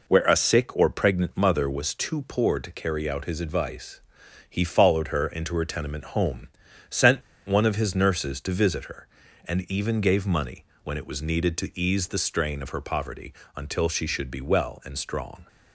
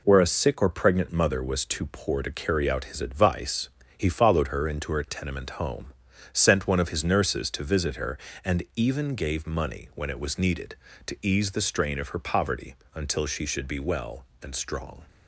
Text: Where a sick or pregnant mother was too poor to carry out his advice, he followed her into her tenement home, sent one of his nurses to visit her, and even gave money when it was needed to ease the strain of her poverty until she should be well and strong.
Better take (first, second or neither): second